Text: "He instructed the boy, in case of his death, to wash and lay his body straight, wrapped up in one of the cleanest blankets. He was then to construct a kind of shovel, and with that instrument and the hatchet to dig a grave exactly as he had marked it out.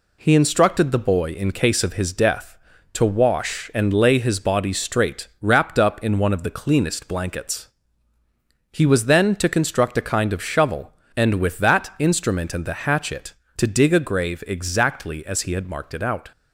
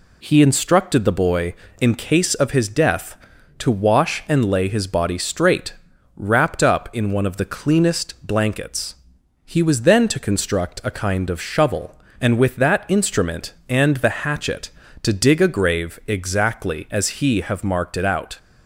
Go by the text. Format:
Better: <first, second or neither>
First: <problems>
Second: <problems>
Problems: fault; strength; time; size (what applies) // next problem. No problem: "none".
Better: first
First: none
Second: says "have" for "had"; at 17.3 s